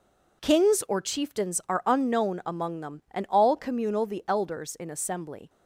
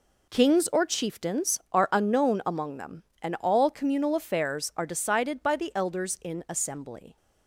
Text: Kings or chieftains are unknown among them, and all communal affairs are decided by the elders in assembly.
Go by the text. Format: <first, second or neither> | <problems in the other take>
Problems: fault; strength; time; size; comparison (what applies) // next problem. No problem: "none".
second | skips "affairs are decided by"; at 4.0 s